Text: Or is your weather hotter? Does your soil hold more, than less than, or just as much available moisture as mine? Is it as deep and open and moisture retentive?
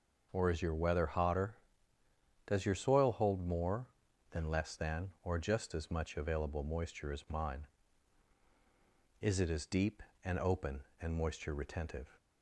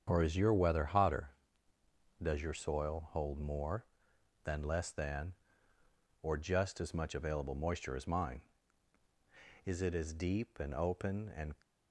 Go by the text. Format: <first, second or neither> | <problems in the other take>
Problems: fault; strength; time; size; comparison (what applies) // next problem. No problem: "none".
first | starts louder than the rest; strong; until 1.0 s; 8 dB // stops before "moisture retentive"; at 11.6 s